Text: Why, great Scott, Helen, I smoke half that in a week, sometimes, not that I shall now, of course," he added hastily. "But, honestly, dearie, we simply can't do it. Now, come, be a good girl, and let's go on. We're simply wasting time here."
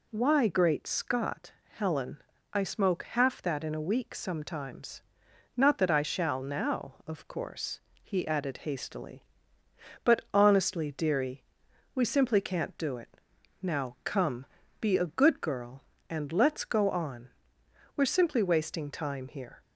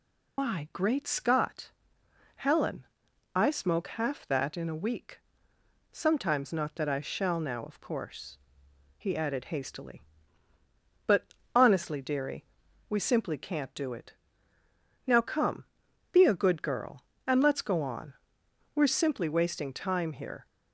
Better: first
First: none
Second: loses the start of "Why"; at 0.3 s; 125 ms

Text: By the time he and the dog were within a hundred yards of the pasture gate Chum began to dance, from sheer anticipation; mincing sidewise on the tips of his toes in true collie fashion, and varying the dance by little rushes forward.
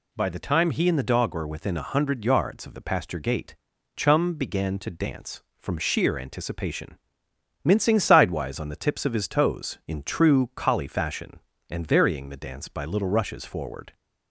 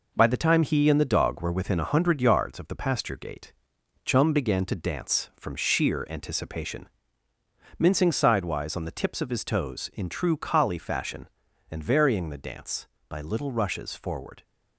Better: first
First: pauses between "gate" and "Chum"; at 3.5 s; 0.40 s long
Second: gets quieter; noticeable; throughout; 5.5 dB // pauses between "gate" and "Chum"; noticeable; at 3.5 s; 0.52 s long

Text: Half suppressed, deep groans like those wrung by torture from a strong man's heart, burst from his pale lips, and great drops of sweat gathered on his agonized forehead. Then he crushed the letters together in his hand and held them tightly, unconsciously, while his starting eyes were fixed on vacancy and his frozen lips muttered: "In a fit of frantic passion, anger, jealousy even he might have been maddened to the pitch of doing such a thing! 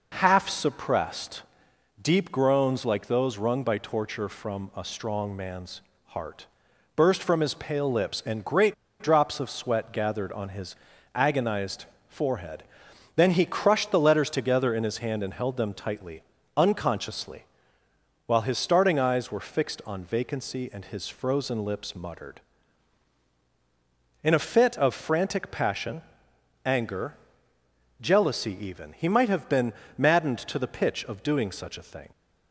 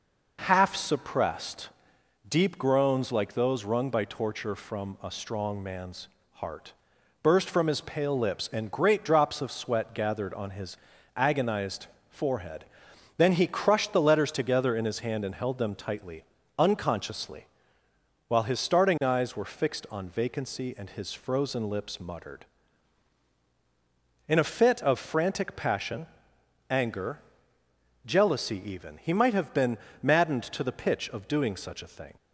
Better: second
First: pauses between "man's" and "heart"; slight; at 5.8 s; 0.26 s long // pauses between "great" and "drops"; slight; at 8.7 s; 0.27 s long // pauses between "his" and "agonized"; at 10.7 s; 0.40 s long // pauses between "agonized" and "forehead"; slight; at 11.8 s; 0.24 s long // pauses between "been" and "maddened"; slight; at 29.7 s; 0.24 s long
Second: pauses between "man's" and "heart"; slight; at 6.0 s; 0.26 s long // pauses between "his" and "agonized"; at 10.7 s; 0.40 s long // pauses between "agonized" and "forehead"; slight; at 11.8 s; 0.24 s long // pauses between "been" and "maddened"; slight; at 29.7 s; 0.24 s long

